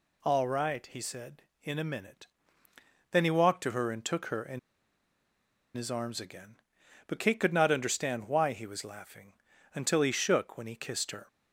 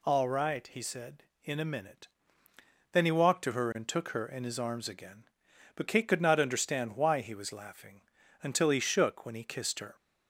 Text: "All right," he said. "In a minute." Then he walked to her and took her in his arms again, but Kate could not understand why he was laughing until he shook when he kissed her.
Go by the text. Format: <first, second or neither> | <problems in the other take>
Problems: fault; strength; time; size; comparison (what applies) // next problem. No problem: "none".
second | pauses between "in" and "his"; at 4.5 s; 1.1 s long // pauses between "laughing" and "until"; at 9.3 s; 0.40 s long; also in the second